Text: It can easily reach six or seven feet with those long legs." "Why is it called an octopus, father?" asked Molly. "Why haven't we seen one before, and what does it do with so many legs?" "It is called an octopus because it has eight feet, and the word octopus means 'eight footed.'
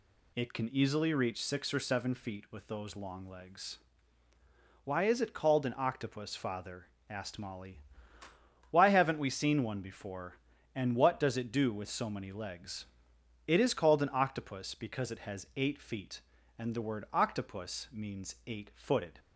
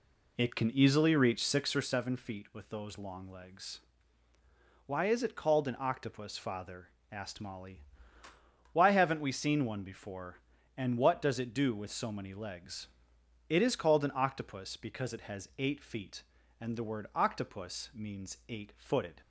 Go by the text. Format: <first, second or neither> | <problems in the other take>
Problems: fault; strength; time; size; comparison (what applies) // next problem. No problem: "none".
first | starts louder than the rest; slight; until 1.9 s; 2.5 dB